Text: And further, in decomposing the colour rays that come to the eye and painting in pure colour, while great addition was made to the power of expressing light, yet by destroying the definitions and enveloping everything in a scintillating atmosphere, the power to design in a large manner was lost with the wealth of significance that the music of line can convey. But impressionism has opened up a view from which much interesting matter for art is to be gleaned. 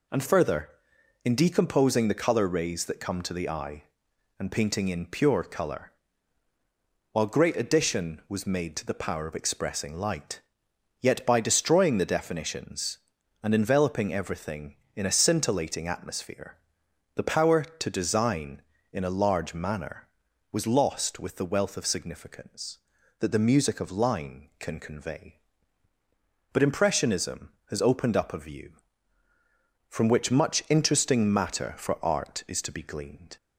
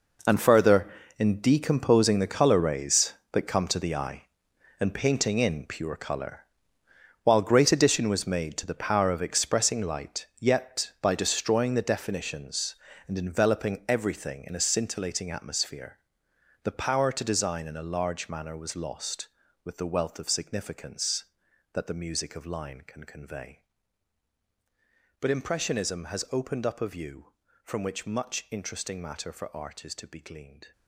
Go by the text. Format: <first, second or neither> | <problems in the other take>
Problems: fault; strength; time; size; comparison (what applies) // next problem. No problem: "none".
first | gets quieter; strong; throughout; 13.5 dB